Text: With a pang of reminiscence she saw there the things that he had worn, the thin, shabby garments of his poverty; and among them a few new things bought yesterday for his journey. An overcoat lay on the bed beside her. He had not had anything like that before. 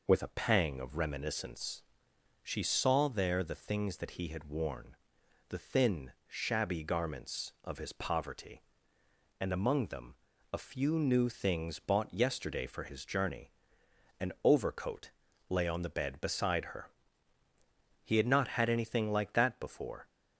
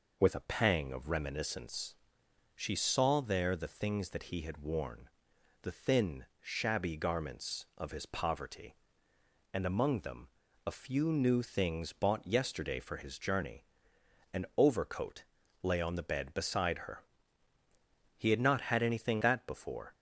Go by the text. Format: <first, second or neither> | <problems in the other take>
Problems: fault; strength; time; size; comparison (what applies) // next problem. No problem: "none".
first | pauses between "reminiscence" and "she"; noticeable; at 1.9 s; 0.62 s long; noticeable in the first // pauses between "them" and "a"; at 10.2 s; 0.40 s long; also in the first // pauses between "overcoat" and "lay"; at 15.2 s; 0.40 s long; also in the first // skips "like"; at 19.2 s